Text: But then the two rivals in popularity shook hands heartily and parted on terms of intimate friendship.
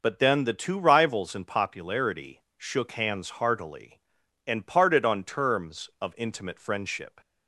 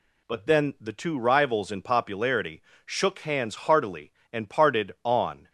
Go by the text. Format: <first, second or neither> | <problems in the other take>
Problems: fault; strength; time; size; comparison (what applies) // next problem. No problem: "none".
first | pauses between "popularity" and "shook"; slight; at 2.6 s; 0.24 s long; slight in the first // stops before "terms of intimate friendship"; at 5.4 s